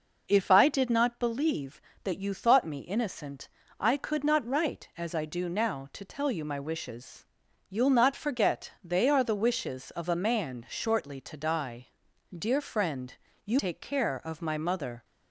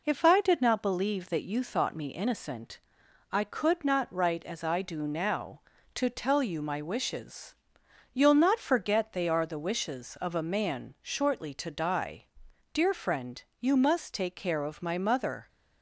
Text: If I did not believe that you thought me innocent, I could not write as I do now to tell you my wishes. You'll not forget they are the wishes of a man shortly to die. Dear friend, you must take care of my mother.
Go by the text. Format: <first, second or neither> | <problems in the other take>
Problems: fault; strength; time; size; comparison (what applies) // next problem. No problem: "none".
second | skips "must"; at 13.5 s